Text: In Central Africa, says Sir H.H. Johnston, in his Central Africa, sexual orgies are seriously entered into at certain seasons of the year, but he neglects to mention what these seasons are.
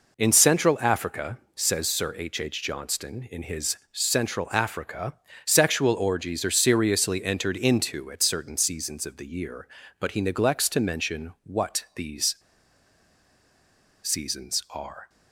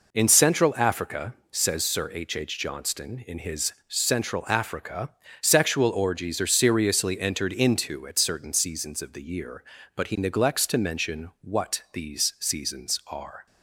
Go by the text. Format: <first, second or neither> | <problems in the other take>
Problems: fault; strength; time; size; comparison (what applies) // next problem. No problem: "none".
second | pauses between "these" and "seasons"; strong; at 12.3 s; 1.6 s long